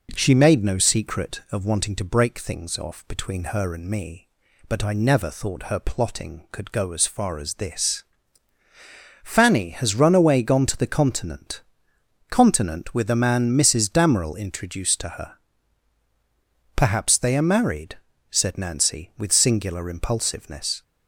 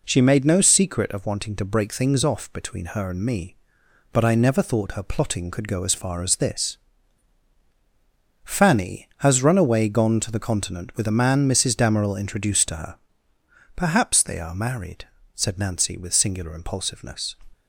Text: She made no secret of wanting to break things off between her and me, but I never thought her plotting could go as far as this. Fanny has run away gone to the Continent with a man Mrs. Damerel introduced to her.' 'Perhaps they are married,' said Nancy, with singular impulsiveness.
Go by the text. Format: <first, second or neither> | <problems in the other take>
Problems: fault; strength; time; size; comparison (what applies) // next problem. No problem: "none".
second | says "Continent" twice; at 12.2 s